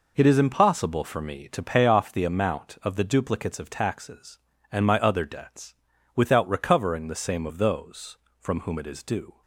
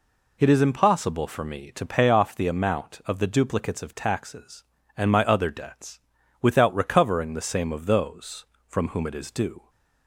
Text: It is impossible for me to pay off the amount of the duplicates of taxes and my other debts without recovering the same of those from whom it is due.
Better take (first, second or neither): second